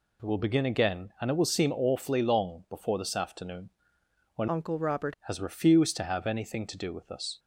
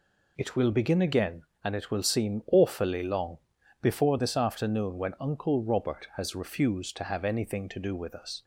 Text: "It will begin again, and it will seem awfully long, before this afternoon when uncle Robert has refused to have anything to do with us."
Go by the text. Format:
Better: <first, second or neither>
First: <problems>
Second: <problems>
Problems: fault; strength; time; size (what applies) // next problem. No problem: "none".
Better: second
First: pauses between "afternoon" and "when"; noticeable; at 3.7 s; 0.64 s long // changes voice from "uncle" to "Robert"; from 4.4 to 5.1 s; 0.7 s long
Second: none